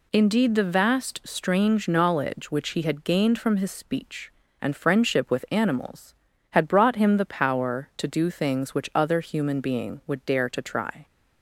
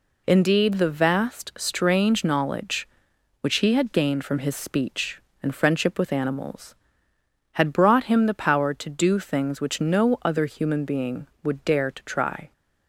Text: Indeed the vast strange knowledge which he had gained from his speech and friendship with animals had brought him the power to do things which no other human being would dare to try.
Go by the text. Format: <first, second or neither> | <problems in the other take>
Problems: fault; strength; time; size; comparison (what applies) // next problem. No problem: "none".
second | skips "no"; at 8.9 s